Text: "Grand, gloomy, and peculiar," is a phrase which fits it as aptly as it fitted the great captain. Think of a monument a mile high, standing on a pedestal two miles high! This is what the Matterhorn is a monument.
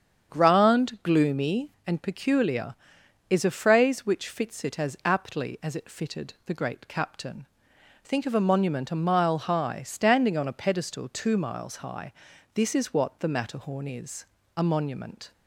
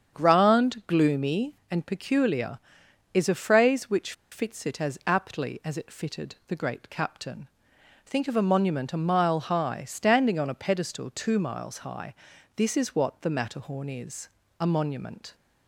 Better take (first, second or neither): first